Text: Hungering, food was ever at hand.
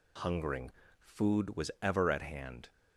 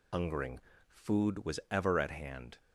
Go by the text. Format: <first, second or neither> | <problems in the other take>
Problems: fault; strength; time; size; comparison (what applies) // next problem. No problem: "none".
first | loses the start of "Hungering"; at 0.1 s; 85 ms